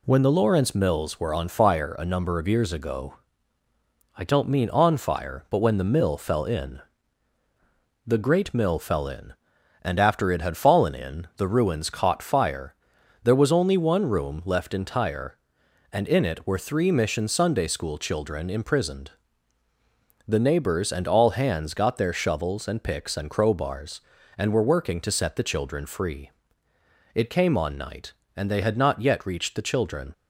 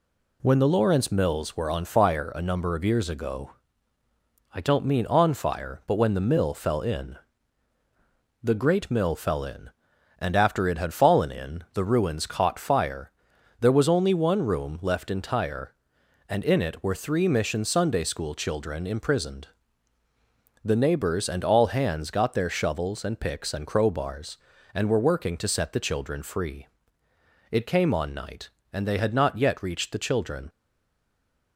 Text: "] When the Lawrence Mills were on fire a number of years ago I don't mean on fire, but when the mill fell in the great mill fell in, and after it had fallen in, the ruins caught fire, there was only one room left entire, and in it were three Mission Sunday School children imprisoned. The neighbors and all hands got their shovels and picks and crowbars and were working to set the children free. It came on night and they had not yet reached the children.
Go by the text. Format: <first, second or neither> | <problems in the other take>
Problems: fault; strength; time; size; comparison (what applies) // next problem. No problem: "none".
first | pauses between "ago" and "I"; at 3.5 s; 1.0 s long; also in the first // pauses between "in" and "the"; at 7.1 s; 1.2 s long; also in the first // stays silent after the last word; from 30.4 s on; 1.1 s long